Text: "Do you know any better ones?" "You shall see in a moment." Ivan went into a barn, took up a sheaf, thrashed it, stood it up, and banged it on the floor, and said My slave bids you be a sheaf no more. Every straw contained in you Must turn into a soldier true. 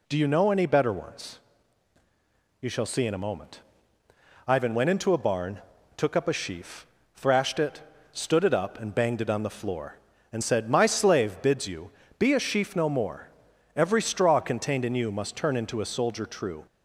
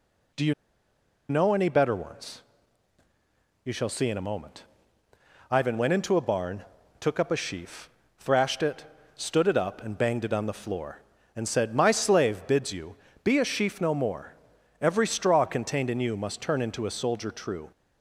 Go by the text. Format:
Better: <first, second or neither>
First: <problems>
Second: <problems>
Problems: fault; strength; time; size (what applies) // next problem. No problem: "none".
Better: first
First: pauses between "you" and "be"; slight; at 11.8 s; 0.30 s long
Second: pauses between "you" and "know"; noticeable; at 0.5 s; 0.76 s long // pauses between "you" and "be"; slight; at 12.9 s; 0.30 s long